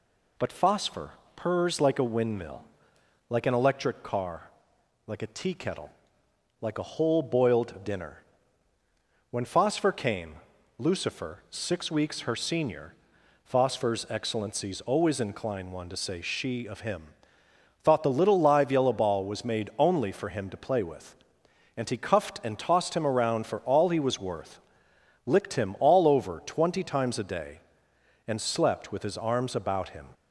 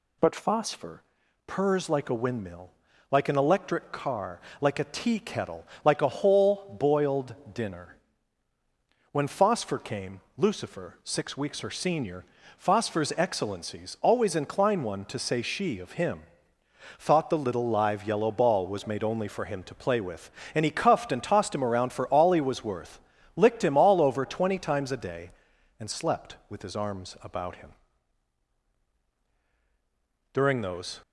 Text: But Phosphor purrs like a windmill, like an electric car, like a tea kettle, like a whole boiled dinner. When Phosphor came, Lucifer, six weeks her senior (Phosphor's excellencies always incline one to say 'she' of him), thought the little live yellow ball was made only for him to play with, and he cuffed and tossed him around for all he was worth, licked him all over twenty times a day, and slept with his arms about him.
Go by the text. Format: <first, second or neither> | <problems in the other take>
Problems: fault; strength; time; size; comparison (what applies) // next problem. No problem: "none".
first | pauses between "Phosphor" and "purrs"; at 1.0 s; 0.44 s long; slight in the first // pauses between "boiled" and "dinner"; slight; at 7.3 s; 0.20 s long // goes on to say "During those"; noticeable; from 30.3 s on; 0.68 s long